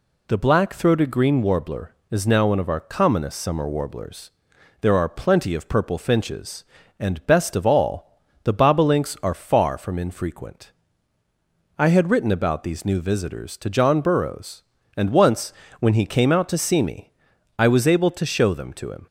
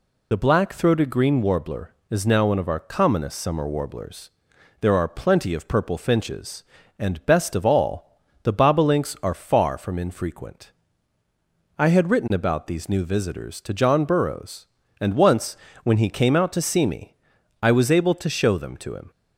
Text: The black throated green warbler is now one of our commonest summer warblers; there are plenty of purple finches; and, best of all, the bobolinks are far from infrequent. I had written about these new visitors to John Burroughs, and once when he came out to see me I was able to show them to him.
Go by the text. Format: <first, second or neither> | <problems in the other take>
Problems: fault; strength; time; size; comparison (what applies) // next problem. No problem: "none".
first | loses the start of "The"; at 0.3 s; 30 ms // pauses between "once" and "when"; slight; at 15.5 s; 0.24 s long; slight in the first // pauses between "me" and "I"; noticeable; at 17.1 s; 0.46 s long; noticeable in the first